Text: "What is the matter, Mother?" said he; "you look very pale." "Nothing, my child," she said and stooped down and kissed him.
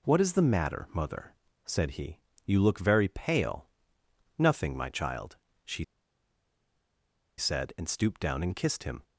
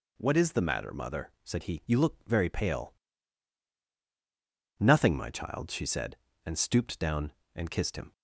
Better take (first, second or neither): second